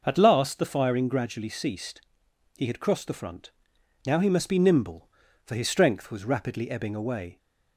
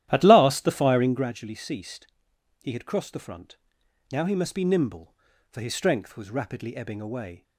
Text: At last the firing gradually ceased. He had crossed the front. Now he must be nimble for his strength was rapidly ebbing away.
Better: first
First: none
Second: starts louder than the rest; strong; until 1.3 s; 12.5 dB

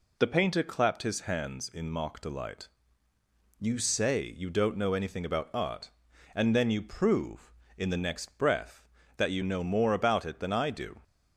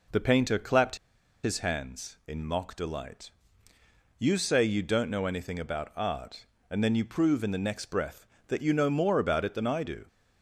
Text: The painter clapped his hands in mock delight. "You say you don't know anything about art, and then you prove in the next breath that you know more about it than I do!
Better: first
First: none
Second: pauses between "clapped" and "his"; noticeable; at 0.9 s; 0.47 s long

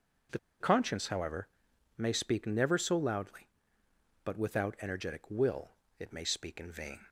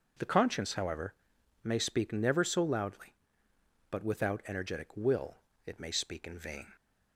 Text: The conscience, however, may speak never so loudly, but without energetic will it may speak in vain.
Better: second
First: pauses between "The" and "conscience"; slight; at 0.3 s; 0.21 s long // pauses between "will" and "it"; slight; at 5.7 s; 0.26 s long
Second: pauses between "will" and "it"; slight; at 5.3 s; 0.26 s long

